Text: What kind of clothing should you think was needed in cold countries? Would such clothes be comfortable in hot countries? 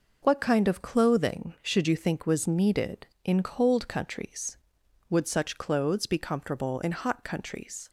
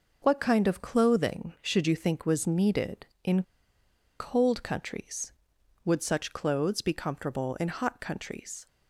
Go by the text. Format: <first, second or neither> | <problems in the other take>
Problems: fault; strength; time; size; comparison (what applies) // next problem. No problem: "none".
first | pauses between "in" and "cold"; noticeable; at 3.4 s; 0.76 s long